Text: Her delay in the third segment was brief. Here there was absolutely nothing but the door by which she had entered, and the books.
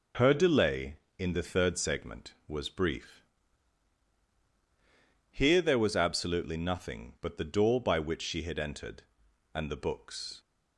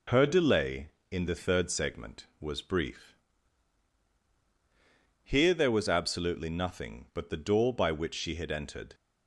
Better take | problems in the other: first | stops before "and the books"; at 8.9 s

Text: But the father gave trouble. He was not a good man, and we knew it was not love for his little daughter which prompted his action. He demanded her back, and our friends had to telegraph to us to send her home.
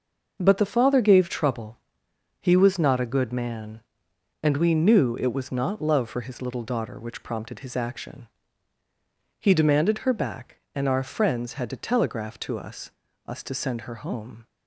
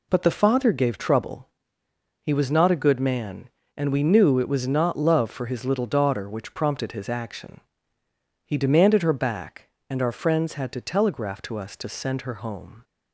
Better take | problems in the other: second | says "us" twice; at 13.2 s

